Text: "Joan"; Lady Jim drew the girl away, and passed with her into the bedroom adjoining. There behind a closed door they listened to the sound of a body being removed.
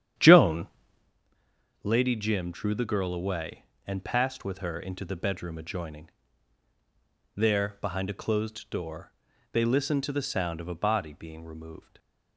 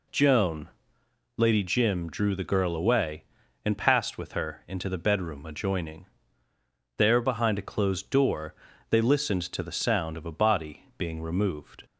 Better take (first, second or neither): second